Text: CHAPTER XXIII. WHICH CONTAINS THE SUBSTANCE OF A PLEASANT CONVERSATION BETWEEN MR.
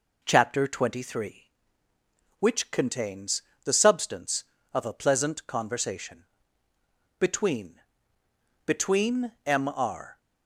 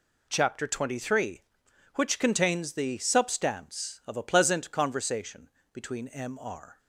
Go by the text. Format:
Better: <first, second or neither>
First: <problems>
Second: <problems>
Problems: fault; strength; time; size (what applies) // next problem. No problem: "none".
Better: second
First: pauses between "CONTAINS" and "THE"; slight; at 3.4 s; 0.24 s long // pauses between "CONVERSATION" and "BETWEEN"; noticeable; at 6.2 s; 0.96 s long // says "BETWEEN" twice; at 8.6 s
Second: pauses between "CONVERSATION" and "BETWEEN"; slight; at 5.4 s; 0.24 s long